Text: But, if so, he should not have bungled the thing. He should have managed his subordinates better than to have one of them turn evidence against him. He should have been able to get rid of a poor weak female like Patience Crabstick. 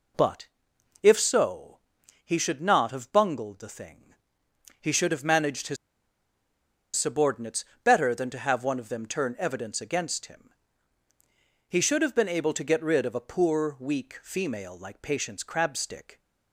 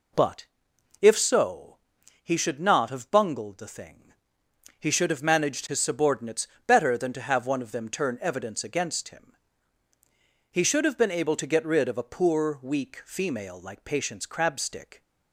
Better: second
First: pauses between "his" and "subordinates"; at 5.7 s; 1.2 s long // pauses between "subordinates" and "better"; slight; at 7.6 s; 0.20 s long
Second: pauses between "subordinates" and "better"; slight; at 6.4 s; 0.20 s long

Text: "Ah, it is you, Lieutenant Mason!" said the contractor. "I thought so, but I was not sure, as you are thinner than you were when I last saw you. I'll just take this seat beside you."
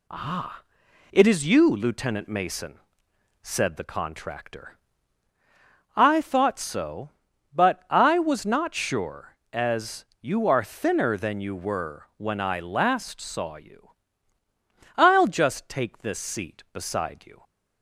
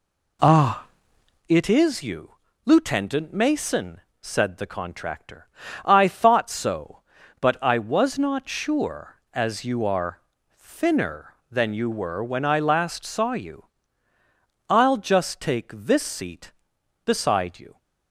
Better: first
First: none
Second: starts louder than the rest; slight; until 1.5 s; 2.5 dB // pauses between "are" and "thinner"; slight; at 10.1 s; 0.34 s long

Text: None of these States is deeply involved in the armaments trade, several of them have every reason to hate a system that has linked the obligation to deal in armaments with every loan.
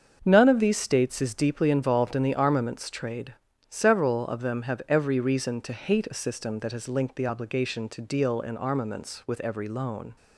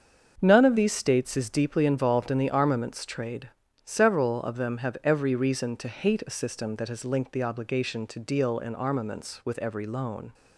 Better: neither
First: starts louder than the rest; until 1.2 s; 7 dB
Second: starts louder than the rest; until 1.4 s; 7 dB

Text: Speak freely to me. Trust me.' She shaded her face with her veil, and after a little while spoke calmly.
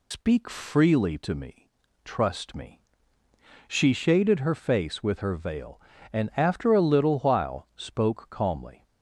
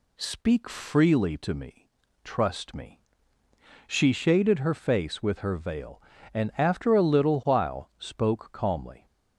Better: second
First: loses the start of "Speak"; at 0.1 s; 115 ms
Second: none

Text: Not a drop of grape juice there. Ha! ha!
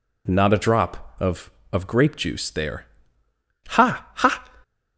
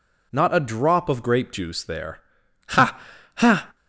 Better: second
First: says "of" twice; at 1.7 s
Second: none

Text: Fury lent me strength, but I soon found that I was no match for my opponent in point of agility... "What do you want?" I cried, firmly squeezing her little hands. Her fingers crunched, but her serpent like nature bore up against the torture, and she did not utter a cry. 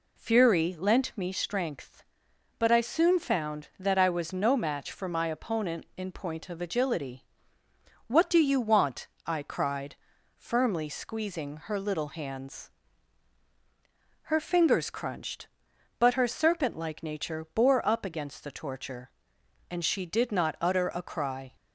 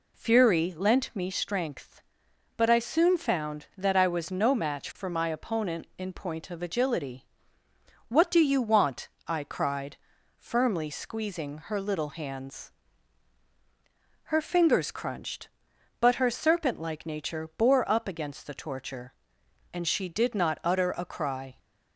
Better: neither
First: none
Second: none

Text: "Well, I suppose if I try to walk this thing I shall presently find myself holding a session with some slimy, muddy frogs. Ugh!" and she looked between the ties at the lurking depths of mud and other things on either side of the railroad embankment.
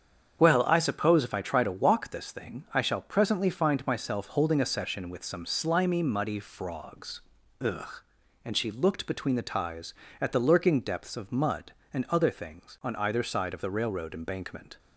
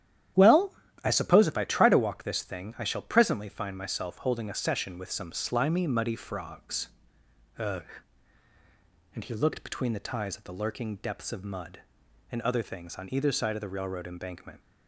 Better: first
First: starts louder than the rest; strong; until 1.4 s; 8 dB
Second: starts louder than the rest; strong; until 1.6 s; 11 dB // says "he" for "she"; at 9.2 s

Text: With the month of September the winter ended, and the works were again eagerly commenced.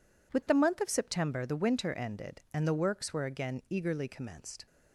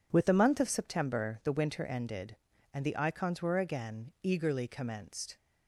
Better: first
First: none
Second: says "icons" for "works"; at 2.9 s

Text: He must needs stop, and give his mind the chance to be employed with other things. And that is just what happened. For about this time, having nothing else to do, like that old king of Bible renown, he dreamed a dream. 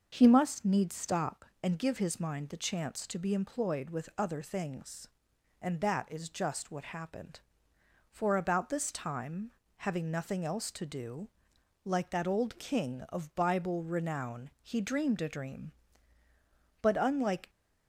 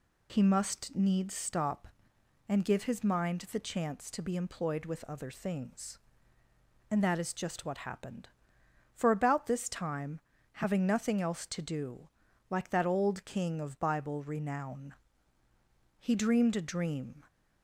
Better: second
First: goes on to say "But unlike"; noticeable; from 16.8 s on; 0.66 s long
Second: none

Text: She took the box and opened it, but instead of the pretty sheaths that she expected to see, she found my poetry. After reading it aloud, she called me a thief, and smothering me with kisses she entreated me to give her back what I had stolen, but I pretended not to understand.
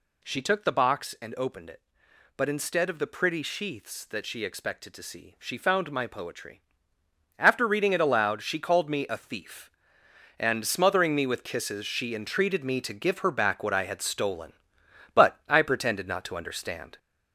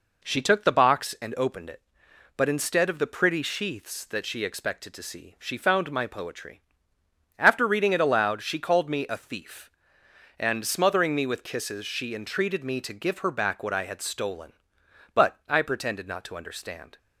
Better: second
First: gets louder; noticeable; throughout; 5 dB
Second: none

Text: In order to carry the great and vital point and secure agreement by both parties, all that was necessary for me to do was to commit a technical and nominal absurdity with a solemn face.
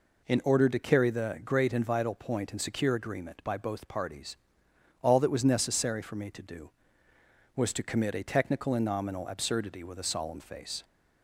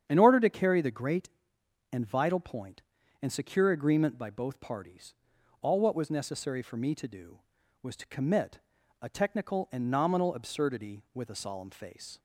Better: first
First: none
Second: starts louder than the rest; strong; until 1.1 s; 8.5 dB // says "what" for "that"; at 5.8 s // pauses between "commit" and "a"; at 8.5 s; 0.42 s long

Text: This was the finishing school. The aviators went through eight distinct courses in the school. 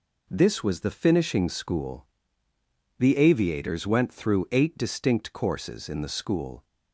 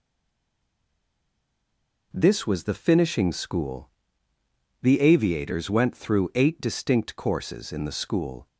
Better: first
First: none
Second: stays silent before the first word; until 2.1 s; 2.1 s long

